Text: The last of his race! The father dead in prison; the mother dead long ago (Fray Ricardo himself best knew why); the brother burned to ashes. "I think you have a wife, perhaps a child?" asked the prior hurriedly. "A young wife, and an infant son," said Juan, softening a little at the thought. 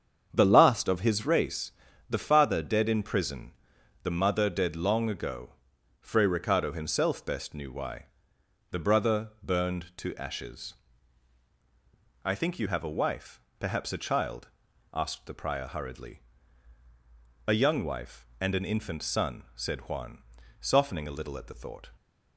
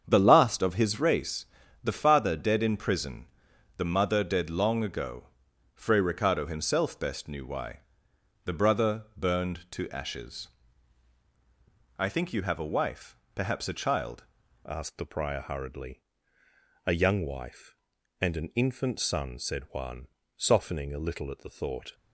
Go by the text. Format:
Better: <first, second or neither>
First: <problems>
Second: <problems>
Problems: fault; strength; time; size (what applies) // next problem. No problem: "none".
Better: first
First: starts louder than the rest; strong; until 1.3 s; 7.5 dB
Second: starts louder than the rest; strong; until 1.0 s; 7.5 dB // changes voice at "asked"; from 14.6 s on; 7.3 s long